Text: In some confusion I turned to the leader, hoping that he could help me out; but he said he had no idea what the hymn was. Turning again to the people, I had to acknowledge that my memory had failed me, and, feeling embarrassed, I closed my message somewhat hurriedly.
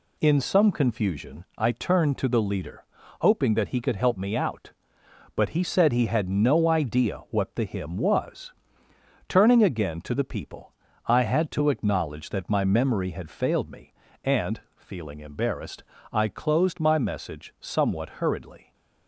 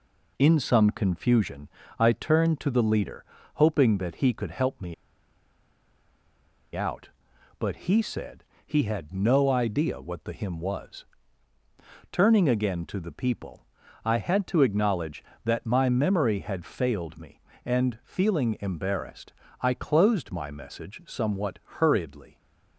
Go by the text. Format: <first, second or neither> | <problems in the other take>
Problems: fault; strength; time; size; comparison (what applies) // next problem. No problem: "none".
first | pauses between "confusion" and "I"; slight; at 1.6 s; 0.28 s long // pauses between "me" and "out"; strong; at 4.9 s; 1.8 s long // pauses between "said" and "he"; slight; at 8.4 s; 0.20 s long